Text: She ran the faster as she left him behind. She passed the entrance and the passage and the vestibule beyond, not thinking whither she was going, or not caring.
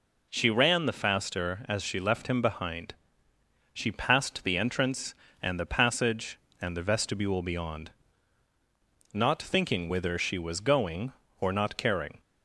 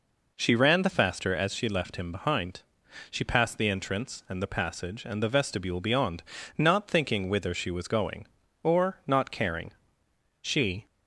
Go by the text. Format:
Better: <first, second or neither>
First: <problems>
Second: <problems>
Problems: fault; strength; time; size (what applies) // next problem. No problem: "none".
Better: first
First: none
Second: goes on to say "She"; slight; from 10.4 s on; 0.44 s long